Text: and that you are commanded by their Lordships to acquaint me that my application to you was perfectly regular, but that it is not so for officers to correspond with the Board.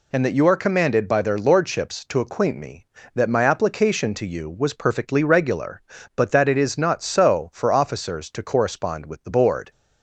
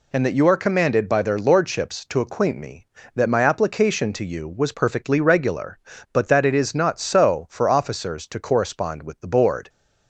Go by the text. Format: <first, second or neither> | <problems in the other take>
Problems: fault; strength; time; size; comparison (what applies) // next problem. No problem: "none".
neither | none